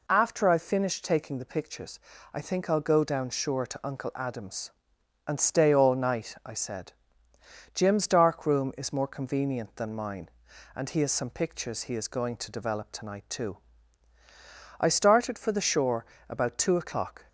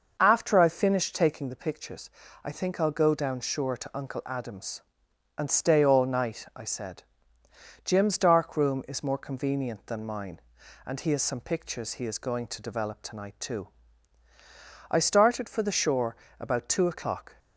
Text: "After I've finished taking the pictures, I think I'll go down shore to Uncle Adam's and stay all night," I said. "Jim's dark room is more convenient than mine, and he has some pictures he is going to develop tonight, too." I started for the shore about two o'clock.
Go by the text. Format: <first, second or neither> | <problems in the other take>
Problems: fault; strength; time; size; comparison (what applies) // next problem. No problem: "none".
first | starts louder than the rest; noticeable; until 1.5 s; 6 dB // pauses between "shore" and "about"; slight; at 16.1 s; 0.24 s long; slight in the first